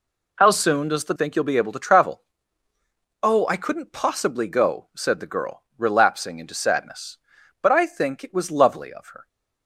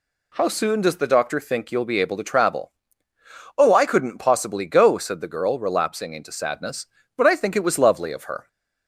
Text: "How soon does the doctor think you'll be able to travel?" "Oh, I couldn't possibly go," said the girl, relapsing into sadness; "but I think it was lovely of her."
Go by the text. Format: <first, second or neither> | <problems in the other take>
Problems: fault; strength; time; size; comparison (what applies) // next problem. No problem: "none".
second | skips "doctor"; at 1.1 s